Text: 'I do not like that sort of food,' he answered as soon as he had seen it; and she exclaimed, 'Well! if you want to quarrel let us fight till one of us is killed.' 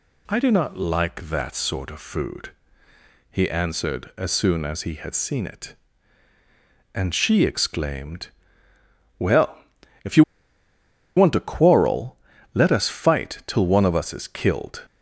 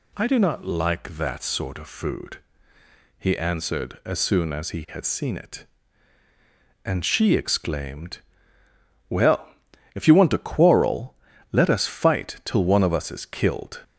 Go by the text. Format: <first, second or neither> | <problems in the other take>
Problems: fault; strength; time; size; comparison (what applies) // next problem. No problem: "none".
second | pauses between "you" and "want"; noticeable; at 10.2 s; 0.93 s long // pauses between "quarrel" and "let"; at 12.1 s; 0.38 s long; also in the second